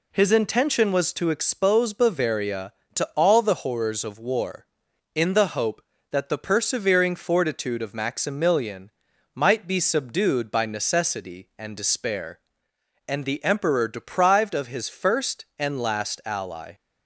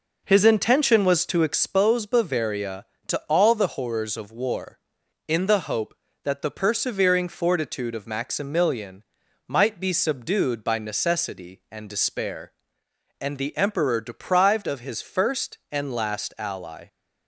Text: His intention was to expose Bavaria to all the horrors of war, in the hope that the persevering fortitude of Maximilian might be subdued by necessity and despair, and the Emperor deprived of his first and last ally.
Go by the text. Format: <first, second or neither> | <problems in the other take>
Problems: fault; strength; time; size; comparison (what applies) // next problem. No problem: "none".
first | starts louder than the rest; noticeable; until 1.9 s; 5 dB // pauses between "Maximilian" and "might"; at 9.0 s; 0.44 s long; also in the first